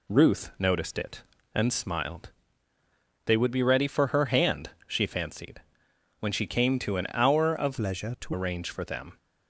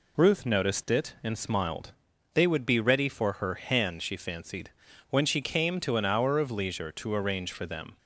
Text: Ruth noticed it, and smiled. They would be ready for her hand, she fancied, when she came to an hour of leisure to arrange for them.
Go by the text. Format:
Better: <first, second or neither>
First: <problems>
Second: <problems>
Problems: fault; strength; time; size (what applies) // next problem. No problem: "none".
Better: second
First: changes voice from "leisure" to "to"; from 7.7 to 8.3 s; 0.6 s long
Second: none